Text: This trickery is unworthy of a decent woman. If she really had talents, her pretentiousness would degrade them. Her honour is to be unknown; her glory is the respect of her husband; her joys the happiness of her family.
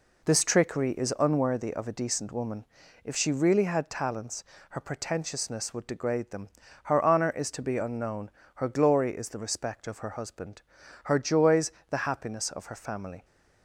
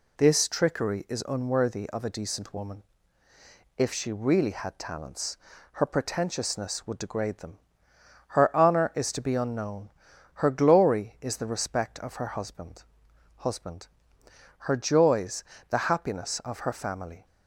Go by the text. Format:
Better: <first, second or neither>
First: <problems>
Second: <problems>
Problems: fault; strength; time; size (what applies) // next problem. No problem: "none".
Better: first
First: pauses between "joys" and "the"; slight; at 11.7 s; 0.18 s long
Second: says "husband" twice; at 13.3 s // pauses between "joys" and "the"; slight; at 15.4 s; 0.26 s long